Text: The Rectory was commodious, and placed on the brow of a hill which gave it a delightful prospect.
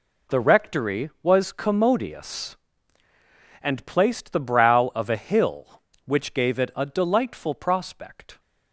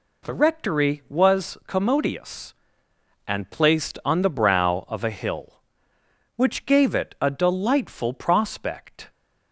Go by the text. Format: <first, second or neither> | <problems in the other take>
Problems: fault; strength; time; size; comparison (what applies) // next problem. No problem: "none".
second | skips "on"; at 4.3 s